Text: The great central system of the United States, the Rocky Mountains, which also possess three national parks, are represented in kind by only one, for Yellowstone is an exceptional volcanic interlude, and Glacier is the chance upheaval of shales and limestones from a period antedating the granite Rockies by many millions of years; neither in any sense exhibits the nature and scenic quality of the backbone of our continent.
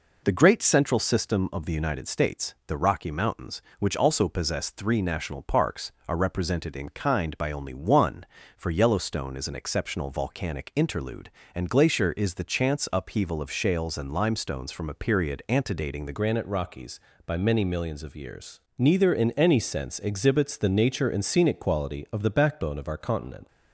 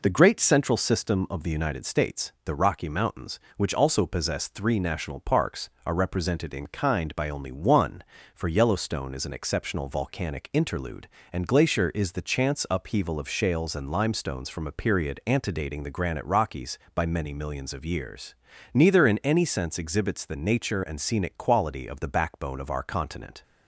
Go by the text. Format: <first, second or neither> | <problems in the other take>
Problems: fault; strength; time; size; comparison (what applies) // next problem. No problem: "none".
second | changes voice at "granite"; from 16.1 s on; 7.3 s long